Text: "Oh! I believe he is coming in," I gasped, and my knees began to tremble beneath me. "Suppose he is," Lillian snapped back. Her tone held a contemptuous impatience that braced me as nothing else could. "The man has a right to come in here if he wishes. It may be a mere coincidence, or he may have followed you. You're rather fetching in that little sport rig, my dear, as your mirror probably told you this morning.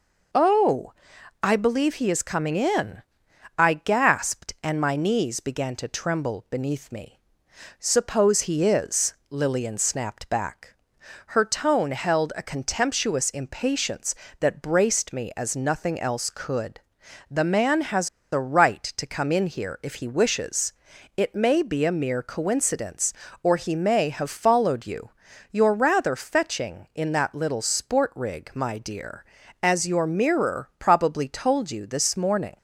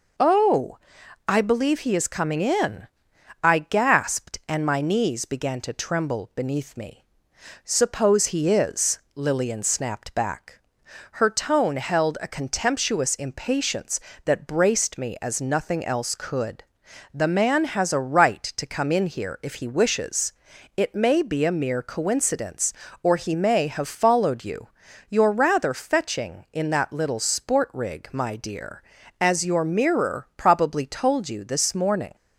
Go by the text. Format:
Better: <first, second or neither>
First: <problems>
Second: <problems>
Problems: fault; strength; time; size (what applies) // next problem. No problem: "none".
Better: second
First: pauses between "has" and "a"; slight; at 18.0 s; 0.24 s long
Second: none